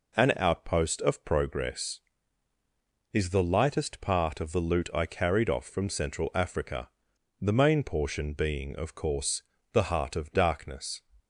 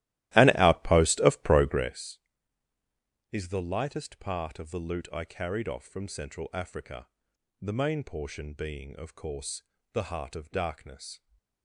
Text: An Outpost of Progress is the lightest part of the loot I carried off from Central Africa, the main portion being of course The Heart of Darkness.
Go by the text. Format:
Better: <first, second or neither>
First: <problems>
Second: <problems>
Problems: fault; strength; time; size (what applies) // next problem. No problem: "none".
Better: first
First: pauses between "course" and "The"; slight; at 9.4 s; 0.30 s long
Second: starts louder than the rest; strong; until 2.0 s; 16 dB // pauses between "course" and "The"; slight; at 9.6 s; 0.30 s long